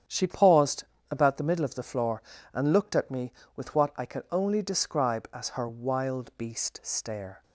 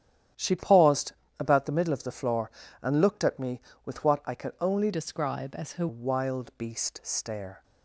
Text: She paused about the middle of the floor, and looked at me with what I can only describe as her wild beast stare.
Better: first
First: starts louder than the rest; strong; until 1.3 s; 9 dB // pauses between "paused" and "about"; slight; at 0.8 s; 0.26 s long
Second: starts louder than the rest; strong; until 1.6 s; 10.5 dB // pauses between "paused" and "about"; slight; at 1.1 s; 0.26 s long // changes voice from "describe" to "her"; from 4.9 to 5.8 s; 0.9 s long

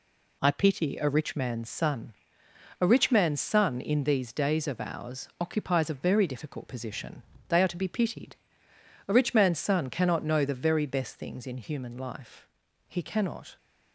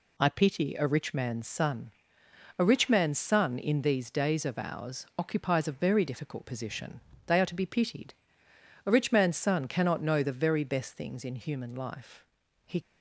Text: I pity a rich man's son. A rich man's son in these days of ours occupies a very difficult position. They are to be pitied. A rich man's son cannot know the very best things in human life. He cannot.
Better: first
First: none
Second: stops before "cannot"; at 12.8 s

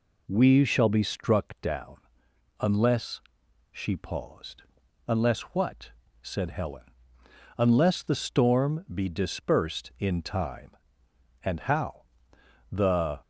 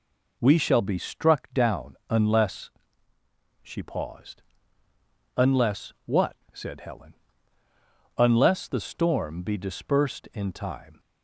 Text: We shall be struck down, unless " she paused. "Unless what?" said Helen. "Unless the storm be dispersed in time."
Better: second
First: goes on to say "And how The"; strong; from 11.4 s on; 1.7 s long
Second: none

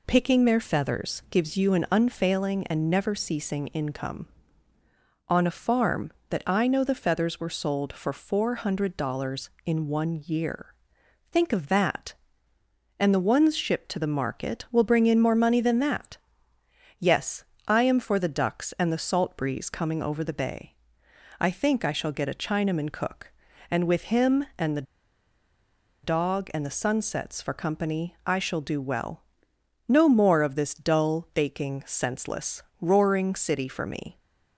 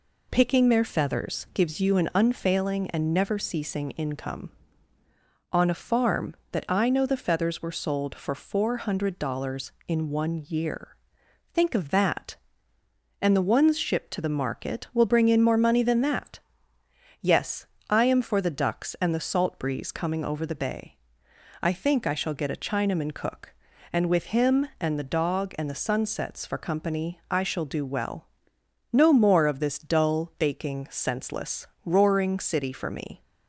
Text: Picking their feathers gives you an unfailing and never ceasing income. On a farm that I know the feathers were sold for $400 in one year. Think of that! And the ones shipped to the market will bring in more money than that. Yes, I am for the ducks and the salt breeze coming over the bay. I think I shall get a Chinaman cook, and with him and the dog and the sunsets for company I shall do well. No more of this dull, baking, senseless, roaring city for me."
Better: second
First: pauses between "the" and "dog"; at 24.8 s; 1.2 s long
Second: none

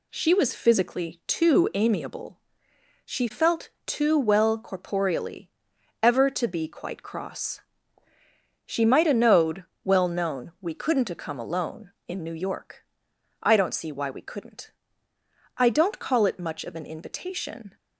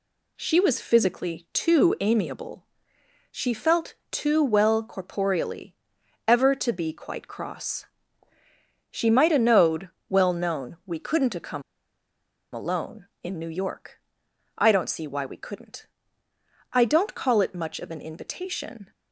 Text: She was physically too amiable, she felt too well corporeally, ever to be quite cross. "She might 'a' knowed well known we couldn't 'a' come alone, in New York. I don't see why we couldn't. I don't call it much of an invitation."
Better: first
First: pauses between "felt" and "too"; slight; at 3.6 s; 0.16 s long // pauses between "knowed" and "well"; slight; at 9.6 s; 0.22 s long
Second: pauses between "felt" and "too"; slight; at 3.9 s; 0.16 s long // pauses between "knowed" and "well"; slight; at 9.8 s; 0.22 s long // pauses between "come" and "alone"; noticeable; at 11.6 s; 0.92 s long

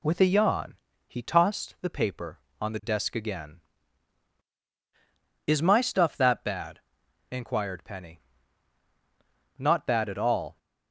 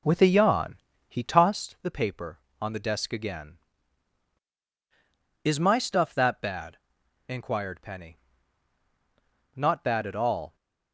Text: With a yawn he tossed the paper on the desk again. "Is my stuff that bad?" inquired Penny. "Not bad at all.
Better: first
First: pauses between "yawn" and "he"; slight; at 0.7 s; 0.32 s long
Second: starts louder than the rest; slight; until 1.7 s; 3 dB // pauses between "yawn" and "he"; slight; at 0.7 s; 0.32 s long

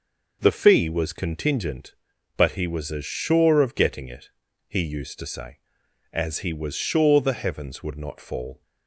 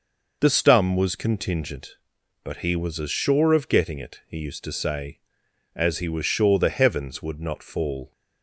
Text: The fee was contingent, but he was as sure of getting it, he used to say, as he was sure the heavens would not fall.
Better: first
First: none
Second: says "stum" for "fee"; at 0.4 s

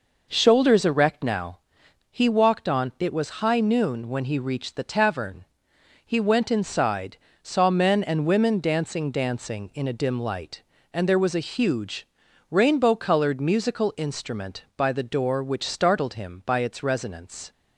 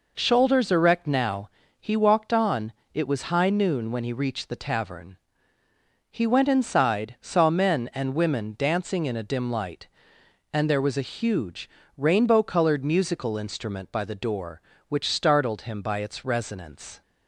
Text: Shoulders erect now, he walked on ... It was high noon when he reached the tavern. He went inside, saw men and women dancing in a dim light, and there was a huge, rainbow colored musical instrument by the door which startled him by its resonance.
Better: second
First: says "dancing" twice; at 9.0 s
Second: none

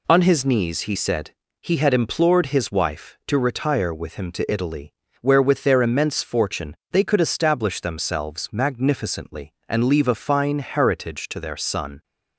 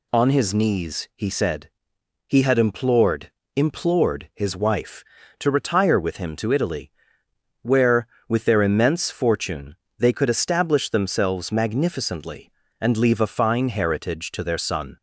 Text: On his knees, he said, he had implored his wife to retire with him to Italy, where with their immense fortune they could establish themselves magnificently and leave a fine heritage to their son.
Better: first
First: pauses between "fortune" and "they"; slight; at 6.7 s; 0.16 s long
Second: says "implored" twice; at 3.5 s // pauses between "fortune" and "they"; slight; at 9.7 s; 0.24 s long

